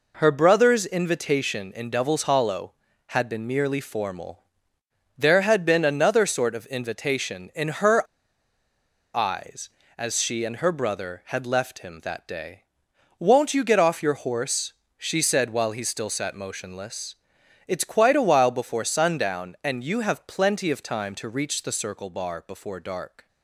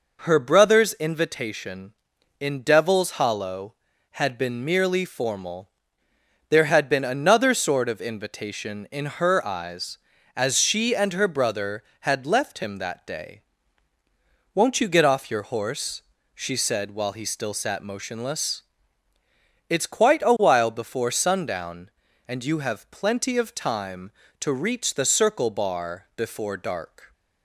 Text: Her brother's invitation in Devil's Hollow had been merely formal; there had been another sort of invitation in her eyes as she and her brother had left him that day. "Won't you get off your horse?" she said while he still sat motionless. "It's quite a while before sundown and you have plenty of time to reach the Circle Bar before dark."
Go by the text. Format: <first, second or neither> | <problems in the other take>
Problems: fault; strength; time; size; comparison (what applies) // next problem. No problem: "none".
second | pauses between "her" and "eyes"; at 8.0 s; 1.1 s long